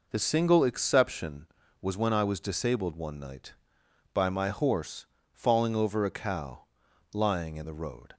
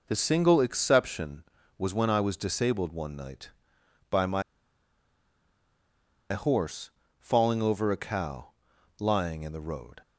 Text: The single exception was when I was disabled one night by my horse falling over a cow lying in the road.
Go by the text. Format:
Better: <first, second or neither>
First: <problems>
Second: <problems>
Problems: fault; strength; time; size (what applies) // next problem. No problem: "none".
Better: first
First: pauses between "horse" and "falling"; slight; at 5.0 s; 0.26 s long // pauses between "cow" and "lying"; noticeable; at 6.6 s; 0.46 s long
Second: pauses between "my" and "horse"; strong; at 4.4 s; 1.8 s long // pauses between "horse" and "falling"; slight; at 6.9 s; 0.28 s long // pauses between "cow" and "lying"; noticeable; at 8.5 s; 0.46 s long